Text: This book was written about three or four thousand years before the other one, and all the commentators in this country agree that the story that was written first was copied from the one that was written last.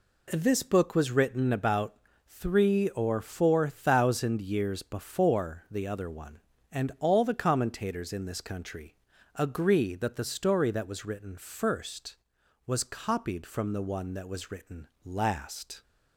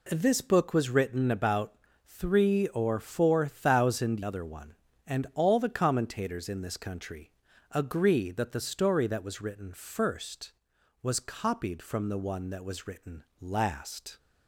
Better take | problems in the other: first | pauses between "about" and "three"; slight; at 1.7 s; 0.32 s long; slight in the first // skips "years before the"; at 4.2 s // pauses between "country" and "agree"; at 7.2 s; 0.42 s long; also in the first // pauses between "written" and "last"; slight; at 13.2 s; 0.18 s long; slight in the first

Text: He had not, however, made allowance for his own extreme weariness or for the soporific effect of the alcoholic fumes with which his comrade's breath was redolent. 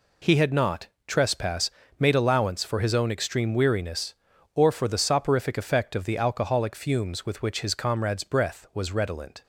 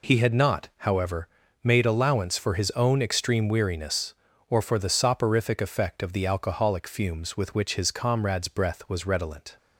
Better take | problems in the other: second | says "trespass" for "however"; at 1.0 s

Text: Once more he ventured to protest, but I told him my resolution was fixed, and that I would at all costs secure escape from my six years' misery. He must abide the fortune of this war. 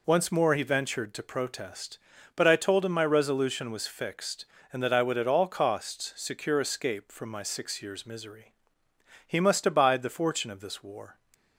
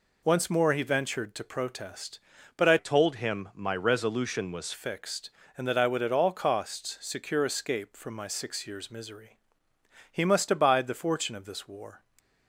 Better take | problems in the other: first | changes voice from "told" to "was"; from 2.7 to 4.7 s; 2.0 s long

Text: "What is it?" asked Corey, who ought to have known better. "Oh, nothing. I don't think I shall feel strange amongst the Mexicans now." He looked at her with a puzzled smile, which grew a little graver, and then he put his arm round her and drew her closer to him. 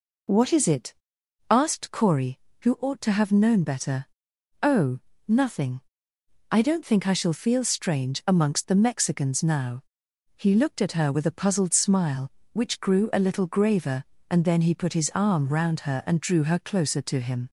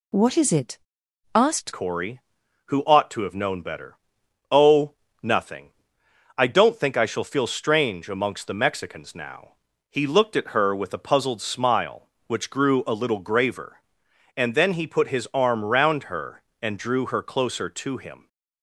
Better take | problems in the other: first | changes voice at "Corey"; from 1.7 s on; 16.5 s long

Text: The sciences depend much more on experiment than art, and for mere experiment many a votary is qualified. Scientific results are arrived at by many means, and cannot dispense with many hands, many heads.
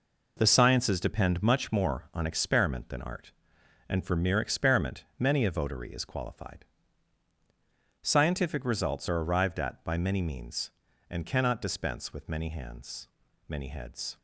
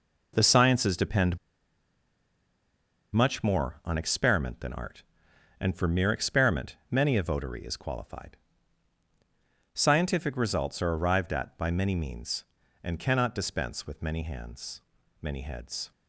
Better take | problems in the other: first | pauses between "depend" and "much"; strong; at 1.3 s; 1.7 s long

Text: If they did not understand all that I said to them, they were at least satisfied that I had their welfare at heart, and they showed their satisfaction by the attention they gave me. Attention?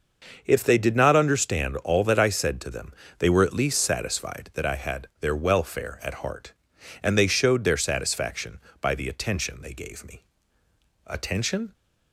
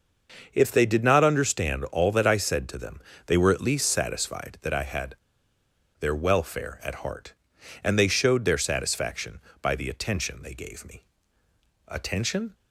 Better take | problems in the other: first | starts louder than the rest; until 1.5 s; 6 dB; also in the first // pauses between "had" and "their"; noticeable; at 5.1 s; 0.85 s long

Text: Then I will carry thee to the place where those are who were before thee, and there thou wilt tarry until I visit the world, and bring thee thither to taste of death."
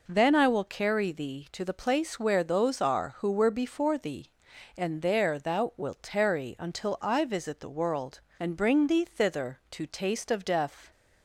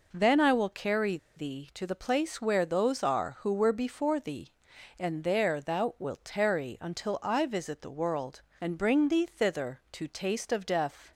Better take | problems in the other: first | pauses between "carry" and "thee"; slight; at 1.1 s; 0.19 s long

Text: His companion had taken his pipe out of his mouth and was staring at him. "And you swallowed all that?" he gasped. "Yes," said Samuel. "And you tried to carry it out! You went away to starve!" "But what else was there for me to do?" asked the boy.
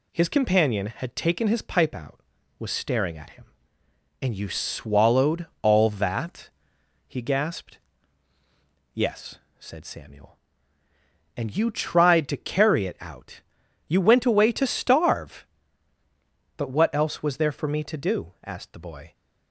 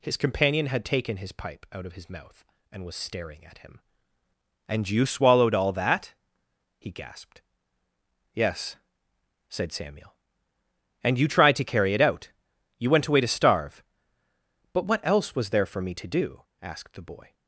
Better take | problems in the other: second | skips "of his mouth and"; at 2.3 s // pauses between "swallowed" and "all"; slight; at 5.4 s; 0.16 s long

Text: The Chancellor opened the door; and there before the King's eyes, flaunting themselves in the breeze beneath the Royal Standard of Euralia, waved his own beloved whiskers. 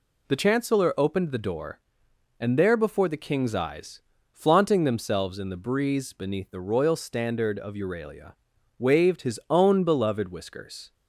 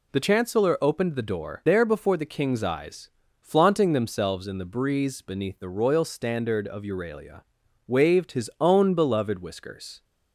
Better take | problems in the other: first | skips "and"; at 1.6 s

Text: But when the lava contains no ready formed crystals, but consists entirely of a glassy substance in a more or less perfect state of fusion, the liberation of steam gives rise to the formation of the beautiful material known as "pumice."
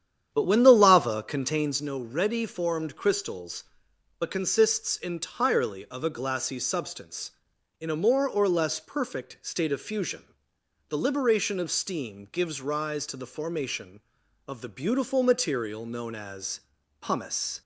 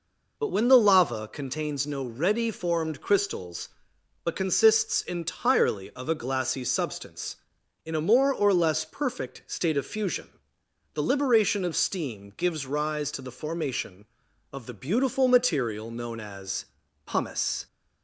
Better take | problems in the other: second | starts louder than the rest; strong; until 1.8 s; 9.5 dB // pauses between "as" and "pumice"; at 16.5 s; 0.40 s long; also in the second

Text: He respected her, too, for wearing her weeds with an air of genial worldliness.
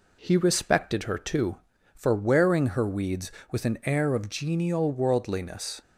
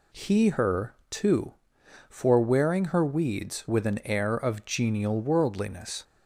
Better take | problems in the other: first | skips "respected"; at 0.4 s

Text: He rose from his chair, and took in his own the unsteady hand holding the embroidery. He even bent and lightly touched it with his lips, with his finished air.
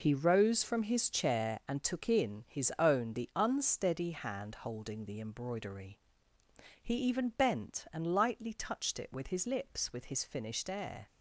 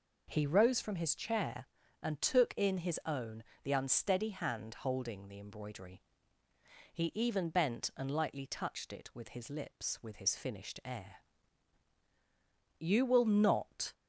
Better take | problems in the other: first | pauses between "own" and "the"; slight; at 3.4 s; 0.22 s long // goes on to say "You will not"; noticeable; from 12.7 s on; 1.1 s long

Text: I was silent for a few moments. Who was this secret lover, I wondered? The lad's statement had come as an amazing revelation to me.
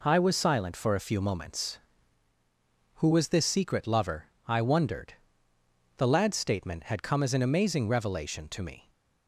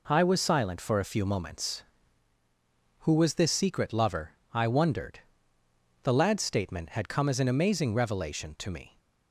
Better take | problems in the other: neither | none

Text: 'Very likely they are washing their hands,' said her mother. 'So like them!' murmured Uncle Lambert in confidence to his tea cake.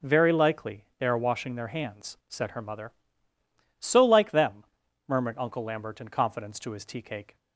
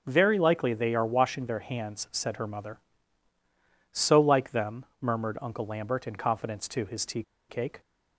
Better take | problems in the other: first | pauses between "tea" and "cake"; slight; at 7.2 s; 0.27 s long

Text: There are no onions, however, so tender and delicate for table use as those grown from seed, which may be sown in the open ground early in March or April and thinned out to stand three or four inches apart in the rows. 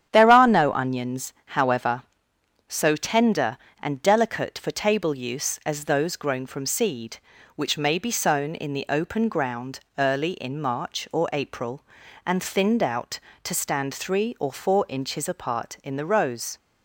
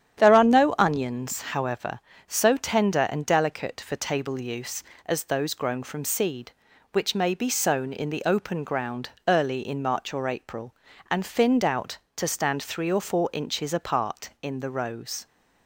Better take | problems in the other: neither | starts louder than the rest; strong; the same in both // pauses between "ground" and "early"; slight; the same in both

